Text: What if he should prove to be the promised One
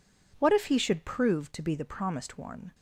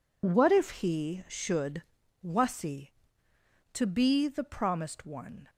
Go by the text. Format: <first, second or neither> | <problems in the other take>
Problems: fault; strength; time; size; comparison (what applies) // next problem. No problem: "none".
first | says "wasi" for "prove"; at 2.2 s